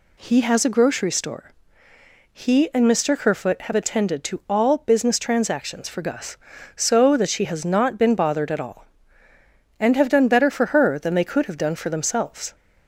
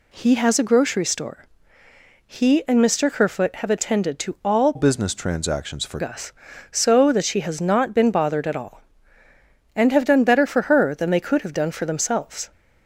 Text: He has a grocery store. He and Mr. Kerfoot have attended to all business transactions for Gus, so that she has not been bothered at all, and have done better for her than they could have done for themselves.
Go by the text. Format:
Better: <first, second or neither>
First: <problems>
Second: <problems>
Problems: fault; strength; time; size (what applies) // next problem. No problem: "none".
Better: first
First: none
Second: changes voice from "business" to "for"; from 4.7 to 5.9 s; 1.2 s long